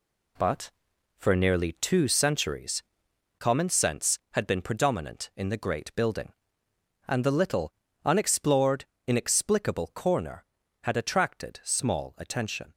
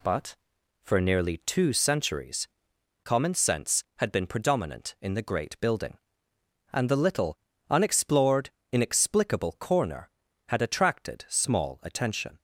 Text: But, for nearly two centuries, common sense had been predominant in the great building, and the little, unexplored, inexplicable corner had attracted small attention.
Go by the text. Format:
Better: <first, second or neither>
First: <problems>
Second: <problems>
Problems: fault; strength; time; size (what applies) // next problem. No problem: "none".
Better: second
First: gets quieter; strong; throughout; 8 dB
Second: none